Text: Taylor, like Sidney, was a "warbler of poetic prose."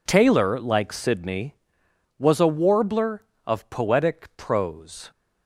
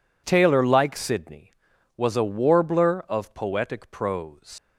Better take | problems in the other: first | leaves "prose" unfinished; at 4.5 s; 125 ms

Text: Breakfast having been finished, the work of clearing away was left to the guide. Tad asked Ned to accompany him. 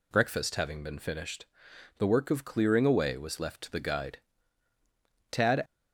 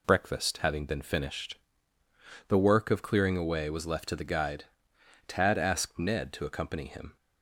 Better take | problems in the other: second | stops before "asked Ned to accompany him"; at 5.6 s

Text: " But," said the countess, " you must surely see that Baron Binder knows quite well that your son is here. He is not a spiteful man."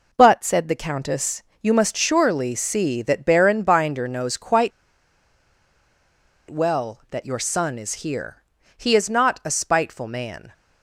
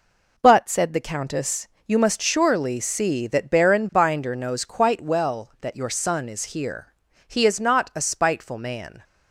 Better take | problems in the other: second | pauses between "quite" and "well"; strong; at 4.7 s; 1.7 s long

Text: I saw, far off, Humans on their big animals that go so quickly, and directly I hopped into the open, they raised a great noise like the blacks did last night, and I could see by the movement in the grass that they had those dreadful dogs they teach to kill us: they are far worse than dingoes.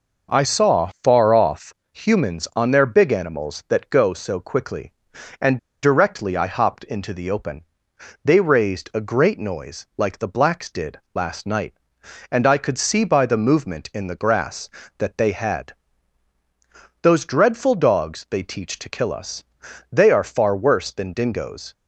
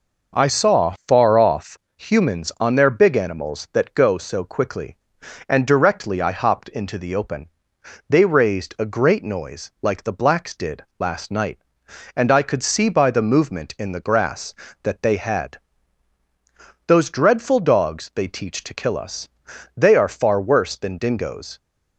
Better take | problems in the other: second | pauses between "and" and "directly"; slight; at 5.5 s; 0.25 s long // pauses between "did" and "last"; slight; at 10.9 s; 0.16 s long; slight in the second // pauses between "had" and "those"; strong; at 15.7 s; 1.2 s long; strong in the second

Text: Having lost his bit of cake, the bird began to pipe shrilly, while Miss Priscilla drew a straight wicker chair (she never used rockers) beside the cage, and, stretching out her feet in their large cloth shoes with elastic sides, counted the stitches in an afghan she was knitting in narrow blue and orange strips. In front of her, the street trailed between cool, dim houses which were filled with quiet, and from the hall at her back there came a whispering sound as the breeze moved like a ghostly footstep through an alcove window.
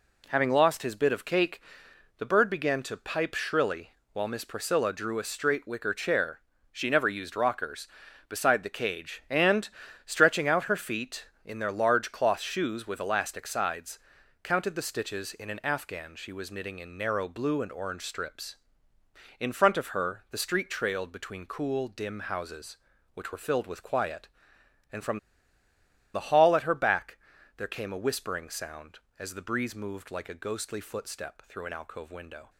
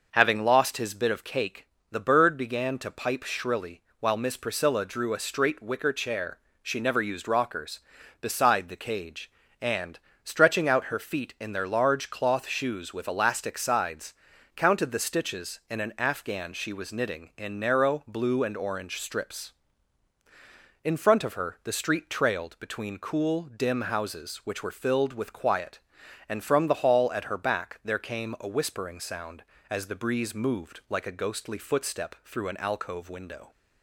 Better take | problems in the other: second | pauses between "from" and "the"; noticeable; at 25.1 s; 0.95 s long // pauses between "back" and "there"; at 27.1 s; 0.40 s long

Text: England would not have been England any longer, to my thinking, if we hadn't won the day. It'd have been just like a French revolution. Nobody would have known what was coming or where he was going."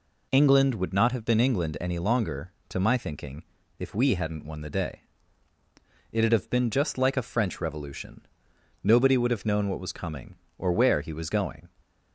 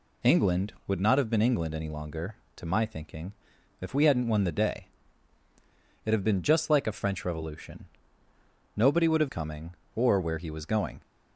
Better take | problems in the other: first | skips "known what was"; at 9.2 s

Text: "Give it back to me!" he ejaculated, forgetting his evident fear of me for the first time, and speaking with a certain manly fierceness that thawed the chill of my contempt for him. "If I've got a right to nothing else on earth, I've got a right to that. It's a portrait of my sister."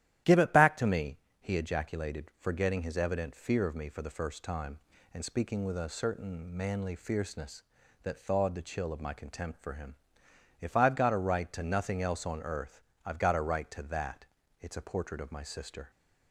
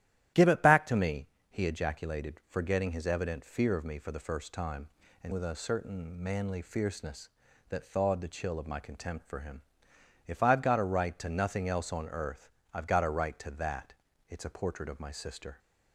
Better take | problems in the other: first | starts louder than the rest; strong; until 1.5 s; 12.5 dB; strong in the first // skips "speaking"; at 5.3 s

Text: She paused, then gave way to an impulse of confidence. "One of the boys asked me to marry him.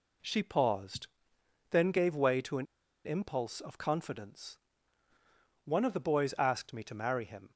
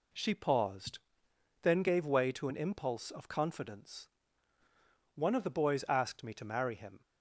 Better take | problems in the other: second | pauses between "an" and "impulse"; at 2.6 s; 0.41 s long

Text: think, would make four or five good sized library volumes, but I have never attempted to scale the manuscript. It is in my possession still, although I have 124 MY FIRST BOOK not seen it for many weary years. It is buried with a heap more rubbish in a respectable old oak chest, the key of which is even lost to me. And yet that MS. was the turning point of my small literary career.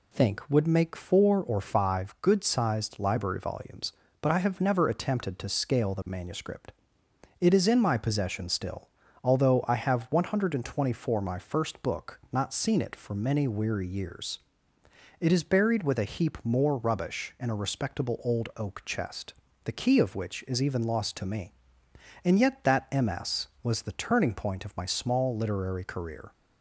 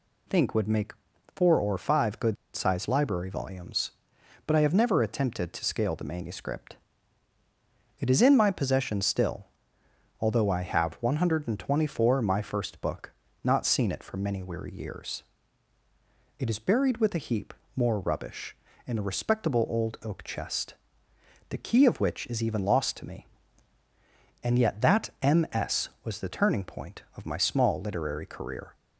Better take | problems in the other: first | pauses between "make" and "four"; at 0.9 s; 0.42 s long // pauses between "good" and "sized"; slight; at 2.3 s; 0.20 s long // pauses between "BOOK" and "not"; slight; at 13.1 s; 0.32 s long // pauses between "heap" and "more"; slight; at 17.5 s; 0.24 s long

